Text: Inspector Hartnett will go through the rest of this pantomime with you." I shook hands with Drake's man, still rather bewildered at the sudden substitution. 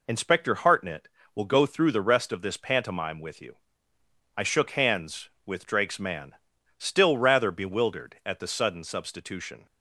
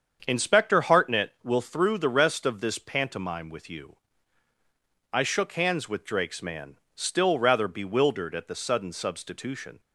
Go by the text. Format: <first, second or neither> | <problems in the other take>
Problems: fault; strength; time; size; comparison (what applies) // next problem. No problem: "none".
first | starts louder than the rest; strong; until 1.2 s; 7.5 dB // skips "go"; at 1.6 s